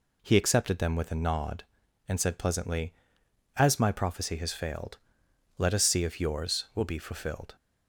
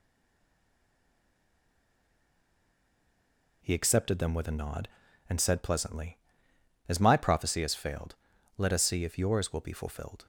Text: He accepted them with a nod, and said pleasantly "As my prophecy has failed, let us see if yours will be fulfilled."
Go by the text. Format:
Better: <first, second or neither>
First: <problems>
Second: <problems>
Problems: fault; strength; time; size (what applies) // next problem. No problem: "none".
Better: first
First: none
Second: stays silent before the first word; strong; until 3.6 s; 3.6 s long